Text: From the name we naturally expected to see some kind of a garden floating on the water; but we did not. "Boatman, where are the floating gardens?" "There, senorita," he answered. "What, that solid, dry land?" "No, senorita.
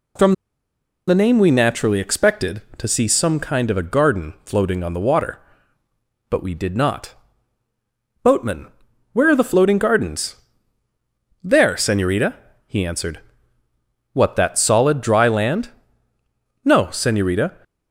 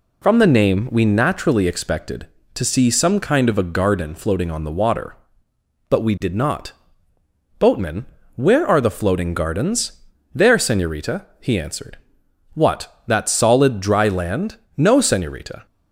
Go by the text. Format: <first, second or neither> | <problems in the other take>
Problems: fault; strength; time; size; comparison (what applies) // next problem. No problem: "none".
second | pauses between "From" and "the"; noticeable; at 0.3 s; 0.75 s long